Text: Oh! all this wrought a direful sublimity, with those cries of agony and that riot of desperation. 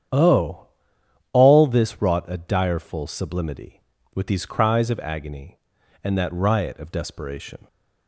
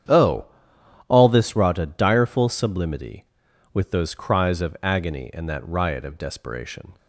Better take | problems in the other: second | starts louder than the rest; strong; until 1.7 s; 9 dB; strong in the second // says "these" for "those"; at 4.2 s

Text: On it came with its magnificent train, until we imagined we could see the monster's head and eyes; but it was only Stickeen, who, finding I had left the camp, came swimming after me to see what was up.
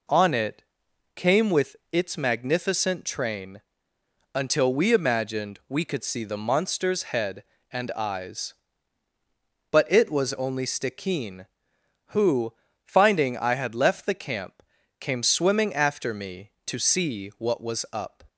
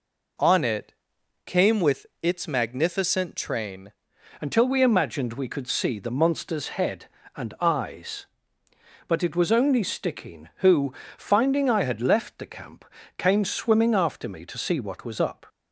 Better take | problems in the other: first | pauses between "it" and "came"; noticeable; at 0.9 s; 0.52 s long; noticeable in the first // pauses between "with" and "its"; slight; at 2.0 s; 0.16 s long; slight in the first // changes voice at "until"; from 4.3 s on; 11.1 s long

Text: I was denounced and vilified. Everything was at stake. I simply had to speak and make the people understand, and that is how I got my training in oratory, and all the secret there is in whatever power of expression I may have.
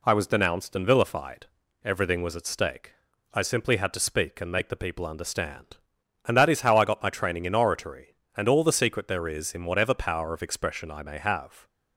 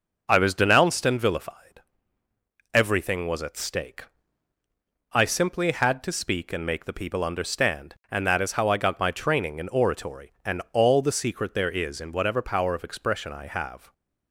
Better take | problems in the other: first | starts louder than the rest; until 1.2 s; 6.5 dB // skips "may"; at 13.4 s

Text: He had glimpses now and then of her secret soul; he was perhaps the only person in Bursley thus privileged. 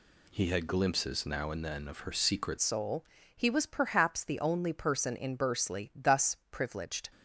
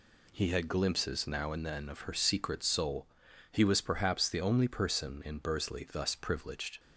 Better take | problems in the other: second | changes voice at "soul"; from 2.6 s on; 4.5 s long // pauses between "thus" and "privileged"; slight; at 6.3 s; 0.16 s long

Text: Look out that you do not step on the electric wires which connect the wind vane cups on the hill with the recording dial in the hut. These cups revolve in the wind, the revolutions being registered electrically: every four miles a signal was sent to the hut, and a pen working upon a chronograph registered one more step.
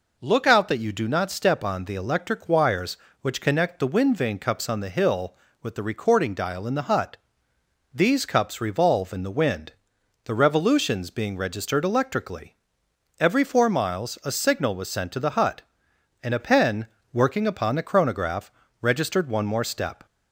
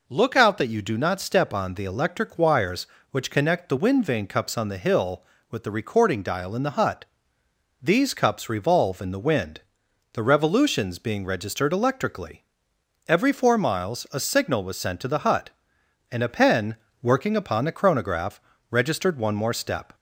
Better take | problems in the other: neither | pauses between "pen" and "working"; slight; the same in both // pauses between "chronograph" and "registered"; slight; the same in both

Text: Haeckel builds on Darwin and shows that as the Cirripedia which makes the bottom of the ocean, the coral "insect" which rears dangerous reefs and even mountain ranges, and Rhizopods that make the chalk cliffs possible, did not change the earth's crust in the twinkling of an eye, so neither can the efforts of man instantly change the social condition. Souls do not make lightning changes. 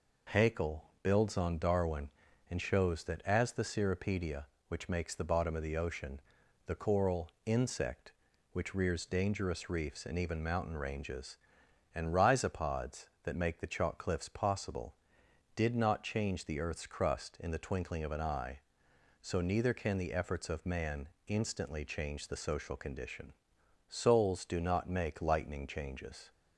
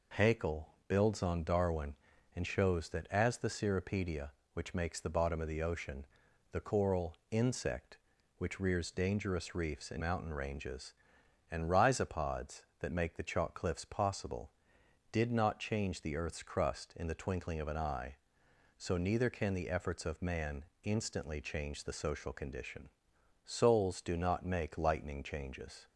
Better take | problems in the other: first | pauses between "Haeckel" and "builds"; slight; at 0.6 s; 0.20 s long; slight in the first // skips "even"; at 10.0 s // pauses between "man" and "instantly"; slight; at 20.6 s; 0.22 s long; slight in the first

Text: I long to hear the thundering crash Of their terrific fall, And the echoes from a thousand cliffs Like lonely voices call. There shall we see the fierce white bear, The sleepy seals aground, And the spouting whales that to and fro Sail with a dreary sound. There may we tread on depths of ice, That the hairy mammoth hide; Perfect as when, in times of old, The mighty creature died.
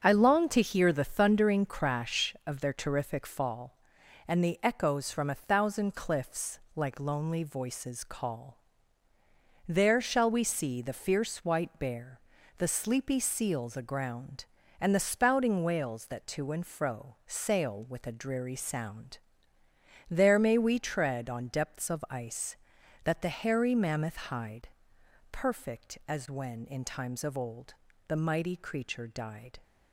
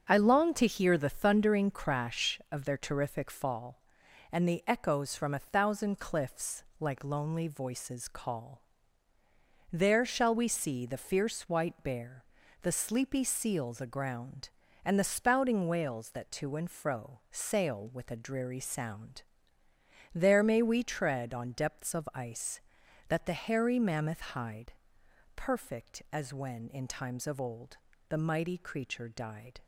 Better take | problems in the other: neither | starts louder than the rest; the same in both // pauses between "cliffs" and "Like"; slight; the same in both

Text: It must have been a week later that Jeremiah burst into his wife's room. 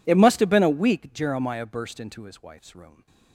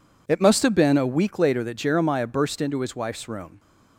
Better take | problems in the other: second | skips "later that"; at 1.1 s

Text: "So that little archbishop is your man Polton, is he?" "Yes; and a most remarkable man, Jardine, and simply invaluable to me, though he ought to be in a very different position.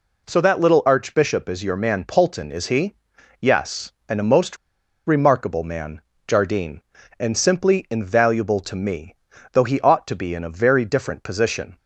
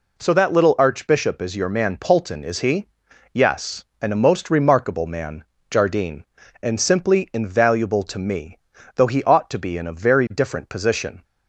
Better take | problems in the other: second | pauses between "most" and "remarkable"; noticeable; at 4.5 s; 0.50 s long

